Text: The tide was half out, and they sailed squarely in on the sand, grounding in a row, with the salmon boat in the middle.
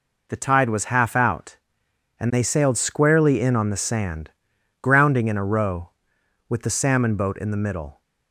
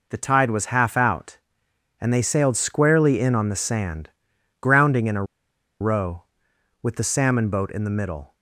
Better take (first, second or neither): first